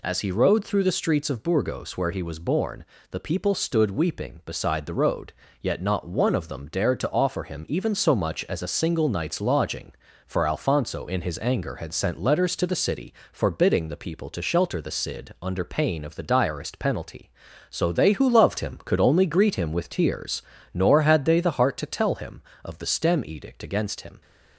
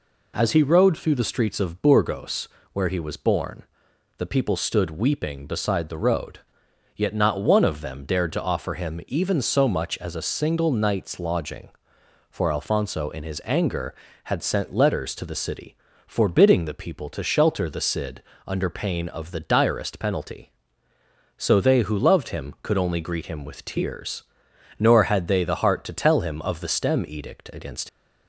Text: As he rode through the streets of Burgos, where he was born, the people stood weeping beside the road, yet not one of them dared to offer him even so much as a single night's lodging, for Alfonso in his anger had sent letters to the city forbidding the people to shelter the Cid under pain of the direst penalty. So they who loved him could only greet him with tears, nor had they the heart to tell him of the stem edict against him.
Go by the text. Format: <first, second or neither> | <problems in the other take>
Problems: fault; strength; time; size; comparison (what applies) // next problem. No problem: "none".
first | pauses between "city" and "forbidding"; slight; at 15.7 s; 0.30 s long; slight in the first // pauses between "Cid" and "under"; slight; at 18.2 s; 0.24 s long // stops before "him"; at 27.8 s